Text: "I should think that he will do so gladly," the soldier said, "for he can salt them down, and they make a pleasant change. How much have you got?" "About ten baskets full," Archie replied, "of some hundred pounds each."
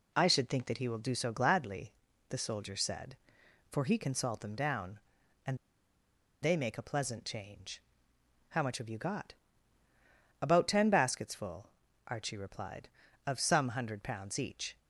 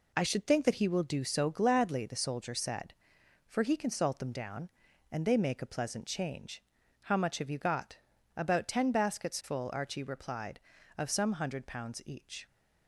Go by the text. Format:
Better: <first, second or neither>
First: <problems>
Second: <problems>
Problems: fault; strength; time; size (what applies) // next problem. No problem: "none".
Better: second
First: pauses between "and" and "they"; noticeable; at 5.5 s; 0.85 s long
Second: none